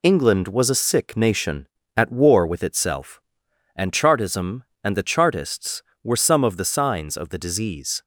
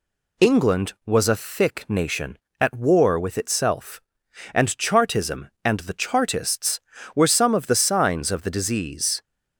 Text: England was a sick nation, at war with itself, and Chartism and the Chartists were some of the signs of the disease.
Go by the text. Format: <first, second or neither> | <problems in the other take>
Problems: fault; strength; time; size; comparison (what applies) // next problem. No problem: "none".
first | says "thick" for "sick"; at 1.3 s